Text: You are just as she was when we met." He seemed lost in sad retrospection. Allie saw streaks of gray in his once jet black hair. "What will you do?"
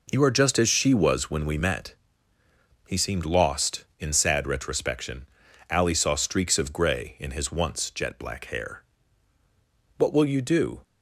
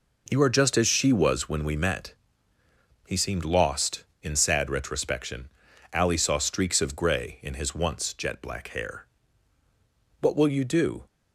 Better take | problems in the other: neither | none

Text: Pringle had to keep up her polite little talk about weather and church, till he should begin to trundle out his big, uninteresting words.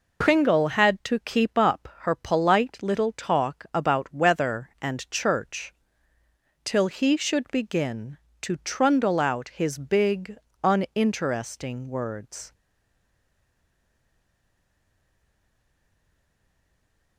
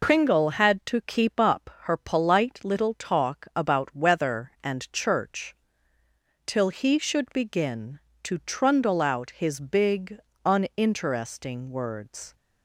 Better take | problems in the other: second | stays silent after the last word; strong; from 12.5 s on; 4.6 s long

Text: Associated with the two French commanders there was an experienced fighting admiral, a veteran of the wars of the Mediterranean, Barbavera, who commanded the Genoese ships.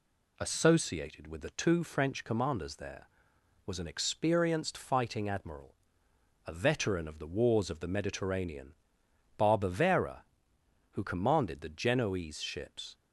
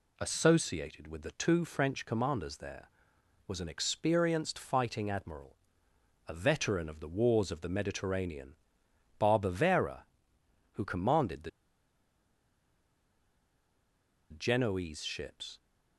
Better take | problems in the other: first | pauses between "the" and "Genoese"; strong; at 11.4 s; 2.8 s long

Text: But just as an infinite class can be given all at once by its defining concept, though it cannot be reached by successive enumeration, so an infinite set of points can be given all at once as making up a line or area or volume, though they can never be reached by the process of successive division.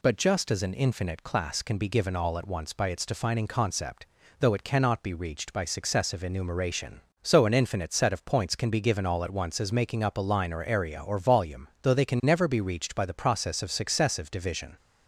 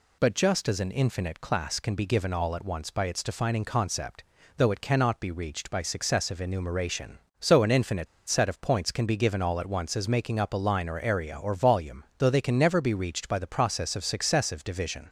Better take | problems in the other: first | pauses between "infinite" and "set"; slight; at 8.0 s; 0.21 s long

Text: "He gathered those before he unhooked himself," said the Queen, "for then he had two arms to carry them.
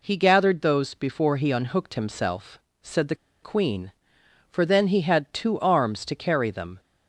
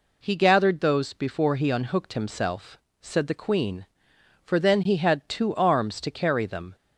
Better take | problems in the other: second | pauses between "the" and "Queen"; slight; at 3.1 s; 0.27 s long

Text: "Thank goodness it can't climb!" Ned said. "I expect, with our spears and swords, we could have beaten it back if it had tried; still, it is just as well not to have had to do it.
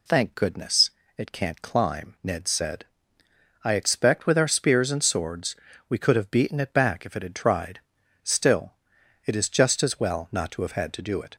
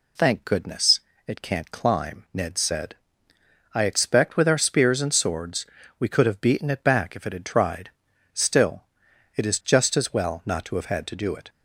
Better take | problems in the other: neither | pauses between "goodness" and "it"; slight; the same in both

